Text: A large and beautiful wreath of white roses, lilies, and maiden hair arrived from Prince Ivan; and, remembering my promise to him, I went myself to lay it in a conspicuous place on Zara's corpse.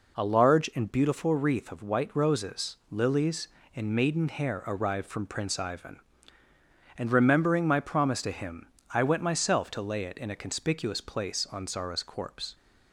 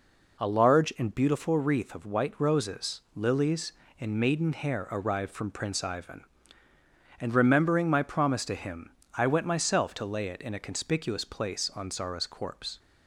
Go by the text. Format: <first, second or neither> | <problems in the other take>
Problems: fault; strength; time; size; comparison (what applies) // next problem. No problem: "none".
neither | none